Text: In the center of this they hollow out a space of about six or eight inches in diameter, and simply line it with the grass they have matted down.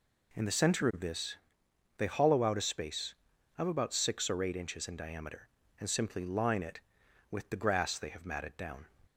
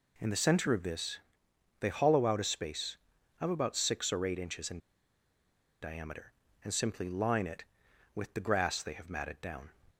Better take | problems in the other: first | pauses between "this" and "they"; noticeable; at 1.1 s; 0.62 s long; noticeable in the first // pauses between "in" and "diameter"; at 4.7 s; 1.0 s long

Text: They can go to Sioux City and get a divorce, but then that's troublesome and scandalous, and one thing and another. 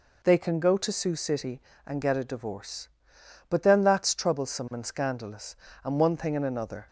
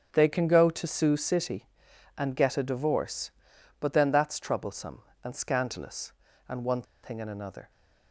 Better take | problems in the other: first | starts louder than the rest; until 1.1 s; 6.5 dB // pauses between "one" and "thing"; slight; at 6.8 s; 0.20 s long

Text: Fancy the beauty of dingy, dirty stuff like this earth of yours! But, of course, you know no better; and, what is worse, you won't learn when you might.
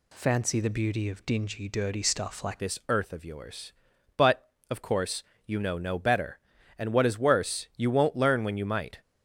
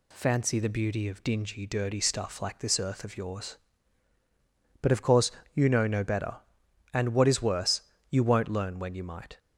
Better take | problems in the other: second | changes voice at "this"; from 2.5 s on; 6.5 s long

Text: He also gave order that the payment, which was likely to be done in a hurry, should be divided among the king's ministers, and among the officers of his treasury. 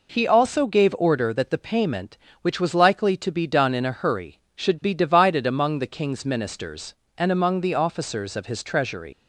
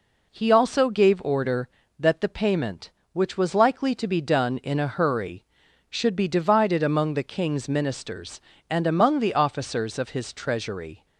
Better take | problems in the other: second | leaves "treasury" unfinished; at 9.1 s; 105 ms

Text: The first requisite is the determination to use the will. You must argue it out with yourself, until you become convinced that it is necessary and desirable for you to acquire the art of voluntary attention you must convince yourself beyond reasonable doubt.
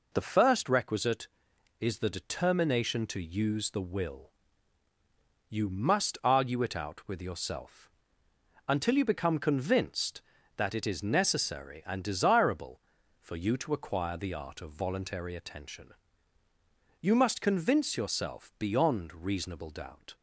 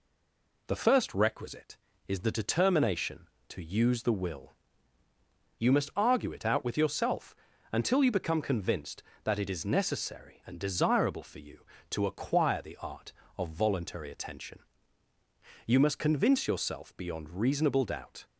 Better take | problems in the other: first | stays silent before the first word; slight; until 0.6 s; 0.6 s long // pauses between "attention" and "you"; at 14.5 s; 1.0 s long; also in the first

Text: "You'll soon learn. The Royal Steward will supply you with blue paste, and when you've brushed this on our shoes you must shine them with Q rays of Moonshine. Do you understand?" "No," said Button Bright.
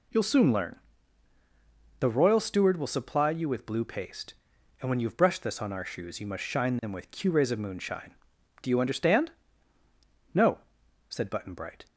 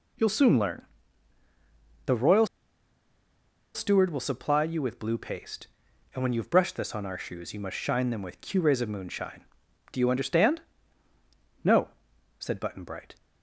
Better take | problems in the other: first | pauses between "Royal" and "Steward"; strong; at 2.4 s; 1.2 s long

